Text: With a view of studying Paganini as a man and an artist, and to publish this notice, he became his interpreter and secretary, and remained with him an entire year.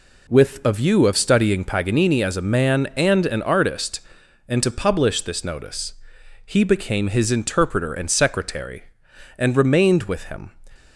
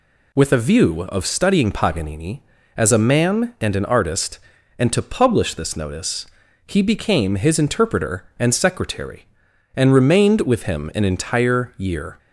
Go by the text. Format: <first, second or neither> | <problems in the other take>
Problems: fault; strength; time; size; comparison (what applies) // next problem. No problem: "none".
second | stops before "an entire year"; at 10.7 s